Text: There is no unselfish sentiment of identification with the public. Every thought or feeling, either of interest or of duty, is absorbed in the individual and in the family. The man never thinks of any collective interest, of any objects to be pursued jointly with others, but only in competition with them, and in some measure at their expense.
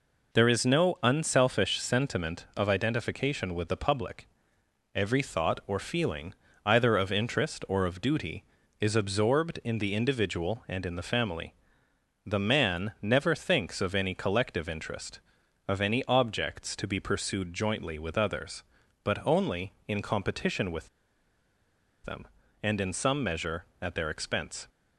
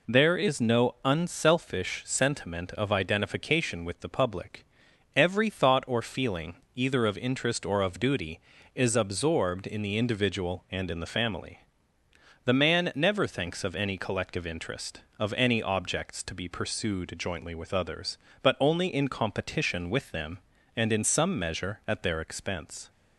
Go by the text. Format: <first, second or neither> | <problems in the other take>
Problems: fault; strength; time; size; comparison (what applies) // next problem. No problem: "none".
second | pauses between "with" and "them"; at 20.8 s; 1.1 s long